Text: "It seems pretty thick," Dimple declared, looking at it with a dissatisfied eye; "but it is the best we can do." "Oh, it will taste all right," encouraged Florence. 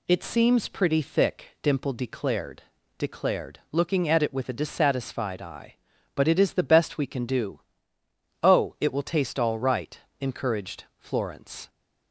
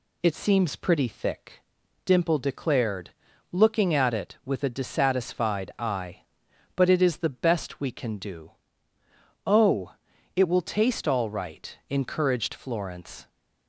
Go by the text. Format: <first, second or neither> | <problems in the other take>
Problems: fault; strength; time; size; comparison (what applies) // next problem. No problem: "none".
second | says "declared" twice; at 2.9 s